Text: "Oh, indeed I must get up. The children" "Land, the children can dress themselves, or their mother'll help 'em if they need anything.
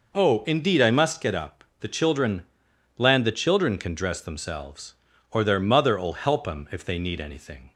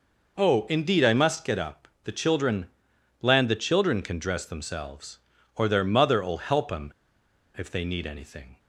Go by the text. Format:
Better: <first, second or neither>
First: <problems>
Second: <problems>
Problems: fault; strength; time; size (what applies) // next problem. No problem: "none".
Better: first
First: pauses between "children" and "Land"; noticeable; at 2.4 s; 0.52 s long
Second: pauses between "children" and "Land"; noticeable; at 2.6 s; 0.52 s long // pauses between "em" and "if"; noticeable; at 6.9 s; 0.65 s long